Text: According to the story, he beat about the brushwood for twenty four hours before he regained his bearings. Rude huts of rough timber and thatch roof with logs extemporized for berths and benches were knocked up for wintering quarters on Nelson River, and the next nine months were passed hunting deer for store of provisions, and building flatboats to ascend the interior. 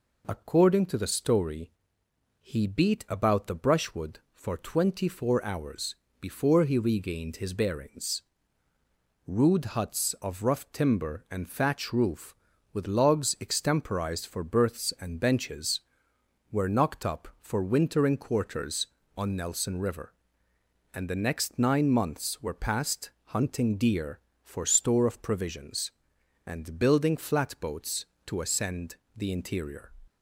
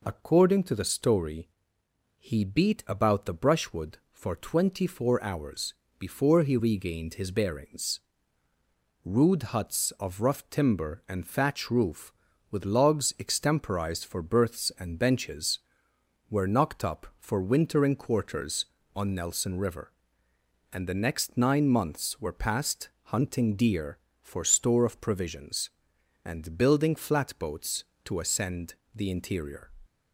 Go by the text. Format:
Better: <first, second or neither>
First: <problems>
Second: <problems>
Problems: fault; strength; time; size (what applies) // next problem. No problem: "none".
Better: neither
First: pauses between "hours" and "before"; slight; at 5.9 s; 0.24 s long // pauses between "passed" and "hunting"; slight; at 23.0 s; 0.16 s long // pauses between "ascend" and "the"; slight; at 28.9 s; 0.18 s long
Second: pauses between "hours" and "before"; slight; at 5.7 s; 0.24 s long // pauses between "passed" and "hunting"; slight; at 22.8 s; 0.16 s long // pauses between "ascend" and "the"; slight; at 28.7 s; 0.18 s long